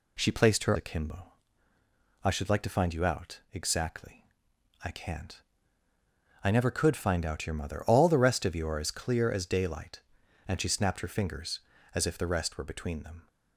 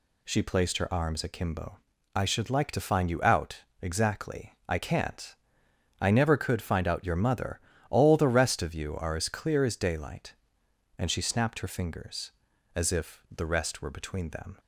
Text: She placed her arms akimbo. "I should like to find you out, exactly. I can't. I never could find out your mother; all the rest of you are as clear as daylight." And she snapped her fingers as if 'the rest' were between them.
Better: second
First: skips "arms"; at 0.7 s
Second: none

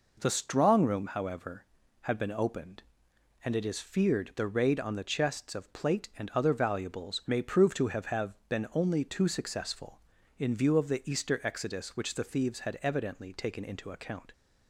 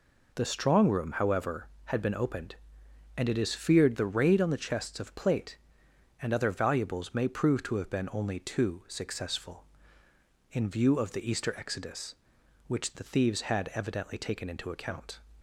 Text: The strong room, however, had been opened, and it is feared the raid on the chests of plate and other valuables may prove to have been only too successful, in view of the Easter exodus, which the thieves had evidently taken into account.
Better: second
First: says "have" twice; at 8.0 s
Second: none

